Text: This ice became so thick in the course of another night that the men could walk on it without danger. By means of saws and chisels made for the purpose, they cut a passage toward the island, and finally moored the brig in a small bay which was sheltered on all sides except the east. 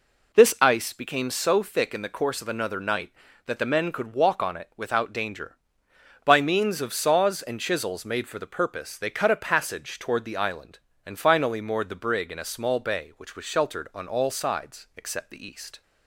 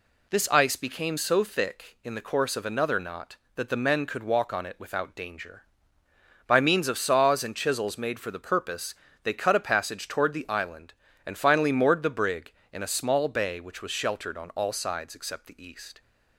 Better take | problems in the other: first | says "knot" for "night"; at 2.9 s

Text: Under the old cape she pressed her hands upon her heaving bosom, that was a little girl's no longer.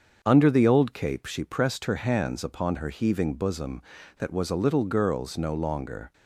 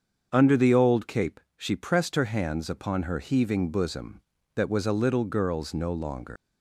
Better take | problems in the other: first | starts louder than the rest; until 1.3 s; 7 dB; also in the first // pauses between "cape" and "she"; slight; at 1.3 s; 0.16 s long // leaves "longer" unfinished; at 6.3 s; 135 ms

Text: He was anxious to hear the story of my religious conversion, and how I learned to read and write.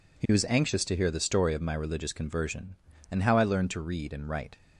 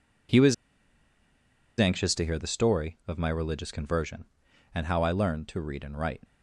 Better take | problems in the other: first | pauses between "was" and "anxious"; at 0.5 s; 1.2 s long

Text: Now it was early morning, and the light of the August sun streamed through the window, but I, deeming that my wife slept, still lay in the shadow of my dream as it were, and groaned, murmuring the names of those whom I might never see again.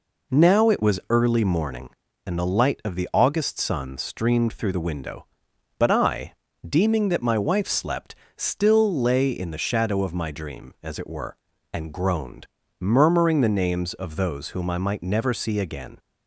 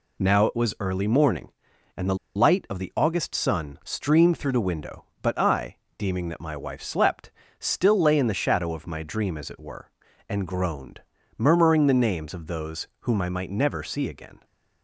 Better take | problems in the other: first | pauses between "the" and "light"; slight; at 2.1 s; 0.20 s long

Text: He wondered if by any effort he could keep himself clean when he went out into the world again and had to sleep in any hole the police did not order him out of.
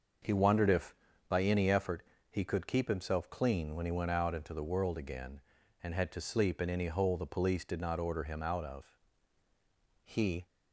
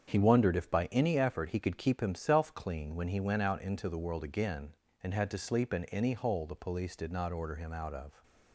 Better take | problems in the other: second | starts louder than the rest; noticeable; until 1.5 s; 6 dB; strong in the second // pauses between "effort" and "he"; slight; at 2.0 s; 0.28 s long // goes on to say "He"; slight; from 10.0 s on; 0.42 s long

